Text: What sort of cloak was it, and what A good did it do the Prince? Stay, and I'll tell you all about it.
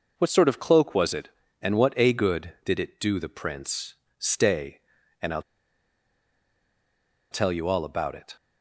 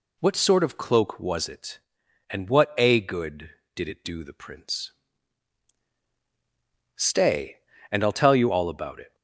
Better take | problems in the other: second | pauses between "I'll" and "tell"; strong; at 5.4 s; 1.8 s long

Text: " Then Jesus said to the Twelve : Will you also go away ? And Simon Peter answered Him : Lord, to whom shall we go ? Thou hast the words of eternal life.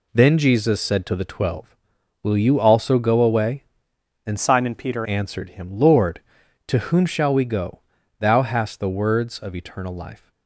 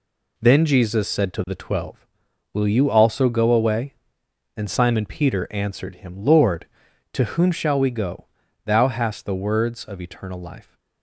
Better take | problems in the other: second | changes voice from "Simon" to "Peter"; from 4.3 to 5.0 s; 0.7 s long

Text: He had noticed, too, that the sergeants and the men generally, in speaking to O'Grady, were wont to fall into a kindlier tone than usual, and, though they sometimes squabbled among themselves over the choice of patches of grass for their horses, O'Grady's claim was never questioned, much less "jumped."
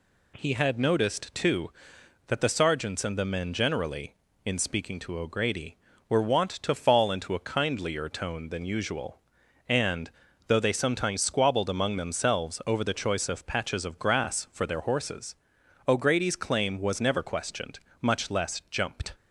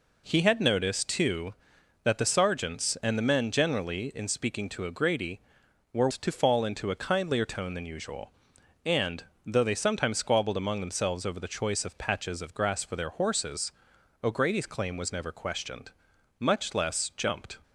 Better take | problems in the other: first | skips "wont"; at 6.1 s

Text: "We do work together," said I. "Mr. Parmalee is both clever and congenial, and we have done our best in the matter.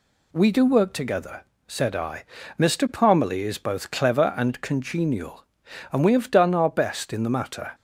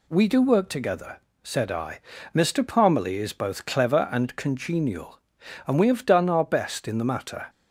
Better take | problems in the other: neither | none

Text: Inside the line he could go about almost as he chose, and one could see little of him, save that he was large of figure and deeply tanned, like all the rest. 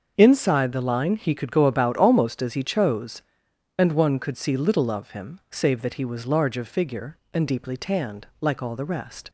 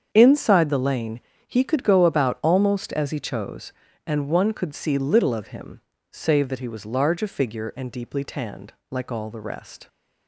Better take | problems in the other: first | starts louder than the rest; strong; until 1.1 s; 7.5 dB; also in the first // says "lane" for "line"; at 0.7 s

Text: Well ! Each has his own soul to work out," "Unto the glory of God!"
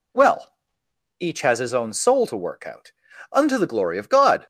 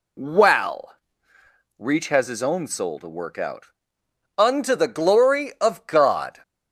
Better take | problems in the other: first | says "Reach" for "Each"; at 1.7 s

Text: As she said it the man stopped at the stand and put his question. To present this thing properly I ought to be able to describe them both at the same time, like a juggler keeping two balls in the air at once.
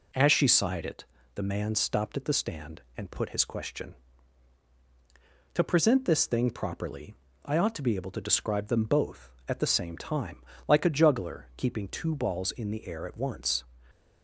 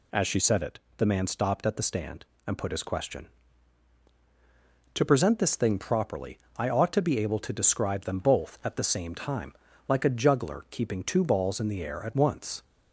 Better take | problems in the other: second | says "sighed" for "said"; at 0.4 s // pauses between "it" and "the"; slight; at 1.0 s; 0.32 s long; slight in the second // pauses between "properly" and "I"; slight; at 7.1 s; 0.30 s long; slight in the second

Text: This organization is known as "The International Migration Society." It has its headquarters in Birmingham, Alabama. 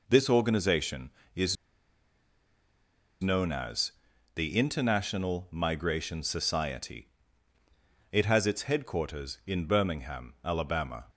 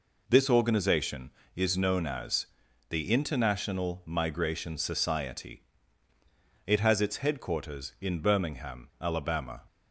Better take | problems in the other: second | pauses between "is" and "known"; strong; at 1.5 s; 1.6 s long // pauses between "as" and "The"; at 3.9 s; 0.42 s long; also in the second

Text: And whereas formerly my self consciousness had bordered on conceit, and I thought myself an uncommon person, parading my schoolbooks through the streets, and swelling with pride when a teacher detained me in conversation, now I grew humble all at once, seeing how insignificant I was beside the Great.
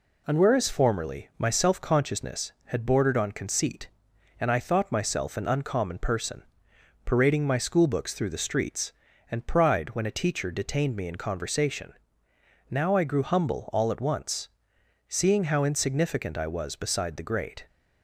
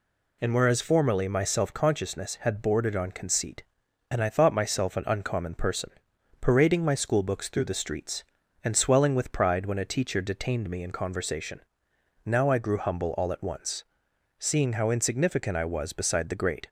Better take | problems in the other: second | skips "swelling with"; at 9.4 s

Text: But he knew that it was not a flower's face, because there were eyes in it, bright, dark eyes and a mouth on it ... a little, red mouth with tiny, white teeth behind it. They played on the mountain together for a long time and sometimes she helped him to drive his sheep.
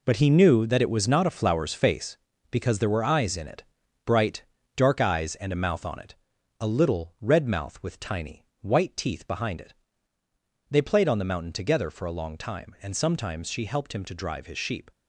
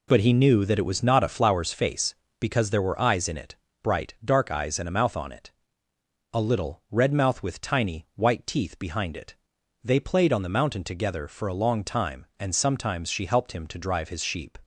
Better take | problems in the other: second | gets quieter; strong; throughout; 10 dB

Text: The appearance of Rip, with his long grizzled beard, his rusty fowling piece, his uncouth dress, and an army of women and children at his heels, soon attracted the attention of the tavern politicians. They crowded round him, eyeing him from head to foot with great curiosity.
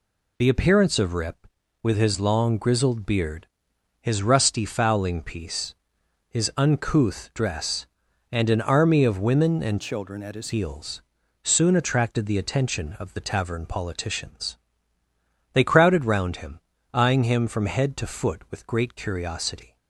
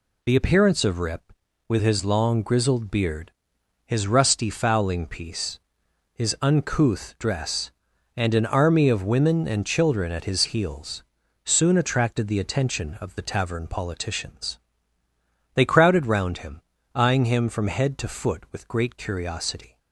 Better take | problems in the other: second | changes voice from "children" to "his"; from 9.8 to 10.5 s; 0.7 s long

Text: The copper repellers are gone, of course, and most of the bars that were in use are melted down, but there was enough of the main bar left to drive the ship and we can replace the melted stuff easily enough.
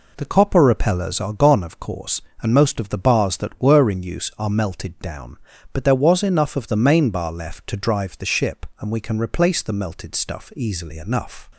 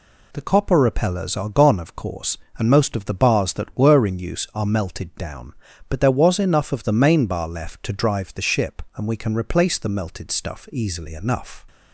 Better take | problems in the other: second | starts louder than the rest; until 1.3 s; 3.5 dB

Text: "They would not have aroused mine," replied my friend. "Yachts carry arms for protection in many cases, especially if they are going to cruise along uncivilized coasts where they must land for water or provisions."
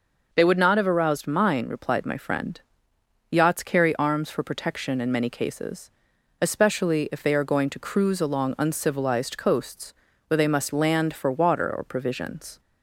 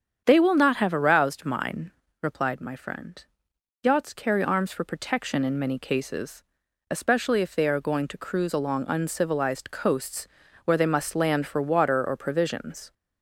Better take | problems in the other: first | starts louder than the rest; strong; until 1.2 s; 8 dB // says "will" for "would"; at 0.3 s // pauses between "coasts" and "where"; slight; at 10.2 s; 0.36 s long; slight in the first

